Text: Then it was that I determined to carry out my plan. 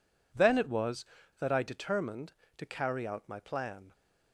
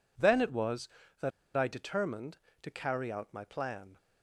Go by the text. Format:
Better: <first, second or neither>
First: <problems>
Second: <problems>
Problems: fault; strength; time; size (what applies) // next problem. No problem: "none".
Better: first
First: none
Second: pauses between "that" and "I"; slight; at 1.3 s; 0.26 s long